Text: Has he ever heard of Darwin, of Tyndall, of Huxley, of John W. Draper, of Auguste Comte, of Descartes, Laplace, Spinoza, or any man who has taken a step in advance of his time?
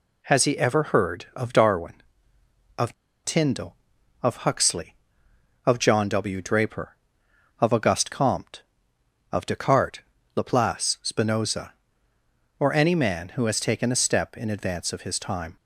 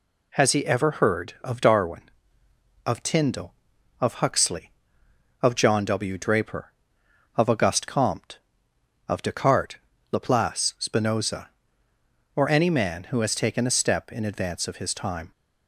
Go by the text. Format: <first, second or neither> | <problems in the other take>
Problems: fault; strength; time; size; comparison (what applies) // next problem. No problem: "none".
second | pauses between "of" and "Tyndall"; slight; at 2.9 s; 0.30 s long